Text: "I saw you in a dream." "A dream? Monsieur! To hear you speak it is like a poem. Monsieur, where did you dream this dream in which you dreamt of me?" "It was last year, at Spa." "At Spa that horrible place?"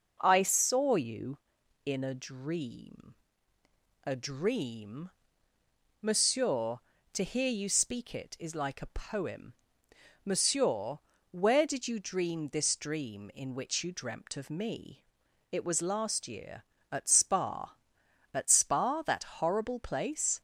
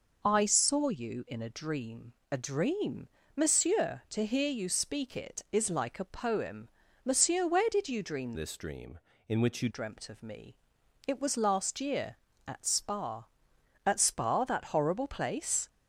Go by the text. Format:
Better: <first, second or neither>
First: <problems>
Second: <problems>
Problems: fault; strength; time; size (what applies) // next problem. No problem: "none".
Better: first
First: none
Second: changes voice from "this" to "you"; from 8.3 to 9.7 s; 1.4 s long